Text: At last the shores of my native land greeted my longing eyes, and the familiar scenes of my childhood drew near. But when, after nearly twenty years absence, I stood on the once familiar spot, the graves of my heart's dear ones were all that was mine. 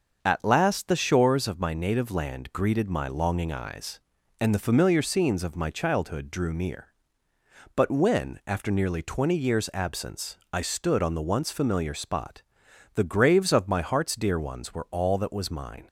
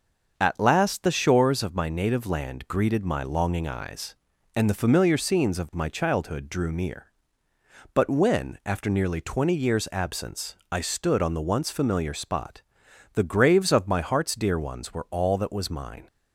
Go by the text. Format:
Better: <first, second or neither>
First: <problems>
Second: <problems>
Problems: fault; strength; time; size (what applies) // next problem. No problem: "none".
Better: neither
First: starts louder than the rest; until 1.2 s; 6 dB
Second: starts louder than the rest; noticeable; until 1.3 s; 6 dB